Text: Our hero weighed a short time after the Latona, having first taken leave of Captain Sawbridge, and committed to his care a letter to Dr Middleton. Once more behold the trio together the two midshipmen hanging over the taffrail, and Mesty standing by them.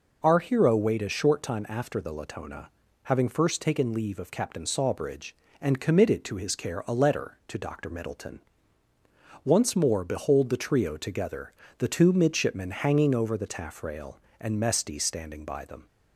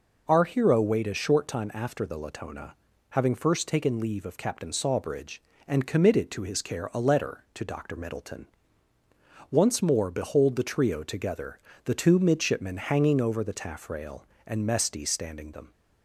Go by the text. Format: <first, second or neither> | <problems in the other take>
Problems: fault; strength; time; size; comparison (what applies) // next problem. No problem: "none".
first | pauses between "together" and "the"; slight; at 11.5 s; 0.26 s long; slight in the first // skips "by"; at 15.5 s